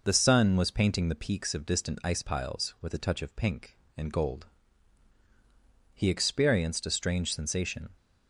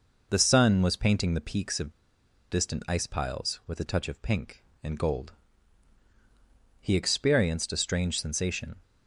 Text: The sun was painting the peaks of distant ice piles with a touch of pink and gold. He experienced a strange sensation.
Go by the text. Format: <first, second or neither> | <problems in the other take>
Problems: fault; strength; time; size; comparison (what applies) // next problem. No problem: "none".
first | pauses between "of" and "distant"; noticeable; at 1.9 s; 0.60 s long